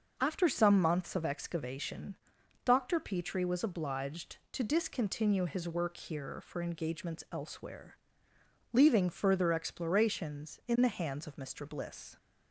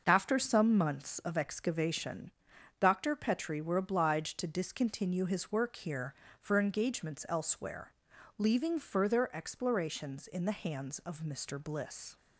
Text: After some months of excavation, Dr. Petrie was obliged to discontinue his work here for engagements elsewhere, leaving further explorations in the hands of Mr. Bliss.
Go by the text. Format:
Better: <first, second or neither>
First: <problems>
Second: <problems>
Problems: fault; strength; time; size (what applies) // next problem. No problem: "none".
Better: first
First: none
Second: starts louder than the rest; noticeable; until 1.1 s; 6 dB // says "were" for "was"; at 3.6 s